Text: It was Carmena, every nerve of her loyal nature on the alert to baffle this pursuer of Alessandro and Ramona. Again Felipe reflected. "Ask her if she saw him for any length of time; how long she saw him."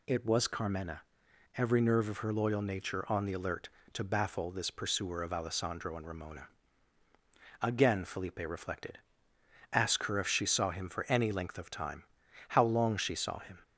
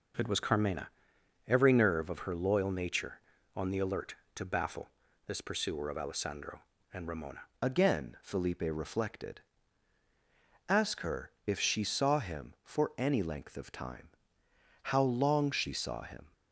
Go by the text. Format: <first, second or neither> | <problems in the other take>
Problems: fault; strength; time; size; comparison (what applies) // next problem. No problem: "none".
first | pauses between "baffle" and "this"; at 4.8 s; 0.40 s long // changes voice at "Again"; from 7.6 s on; 8.7 s long // pauses between "her" and "if"; slight; at 11.2 s; 0.16 s long